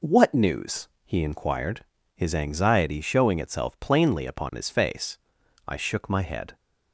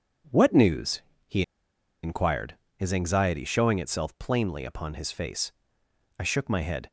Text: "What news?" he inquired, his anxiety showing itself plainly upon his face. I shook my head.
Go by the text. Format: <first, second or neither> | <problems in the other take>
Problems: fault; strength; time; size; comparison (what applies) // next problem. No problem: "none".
first | pauses between "he" and "inquired"; noticeable; at 1.4 s; 0.60 s long